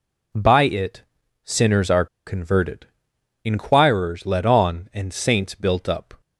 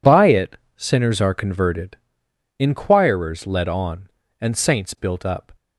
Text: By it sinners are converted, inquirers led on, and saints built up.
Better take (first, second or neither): second